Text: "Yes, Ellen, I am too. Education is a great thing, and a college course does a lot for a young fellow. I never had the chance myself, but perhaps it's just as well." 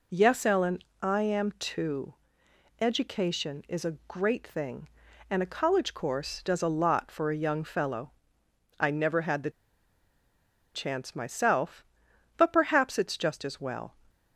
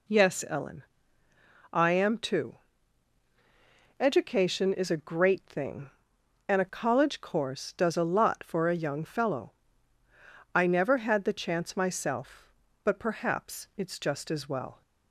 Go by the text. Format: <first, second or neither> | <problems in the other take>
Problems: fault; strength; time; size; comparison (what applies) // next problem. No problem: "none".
second | pauses between "the" and "chance"; strong; at 9.4 s; 1.2 s long